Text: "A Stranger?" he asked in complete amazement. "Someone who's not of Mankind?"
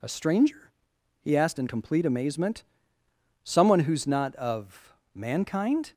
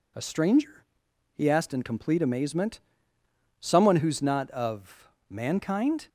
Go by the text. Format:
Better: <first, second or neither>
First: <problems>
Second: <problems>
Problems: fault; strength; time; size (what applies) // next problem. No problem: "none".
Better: neither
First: pauses between "of" and "Mankind"; slight; at 4.9 s; 0.22 s long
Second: pauses between "of" and "Mankind"; slight; at 5.0 s; 0.22 s long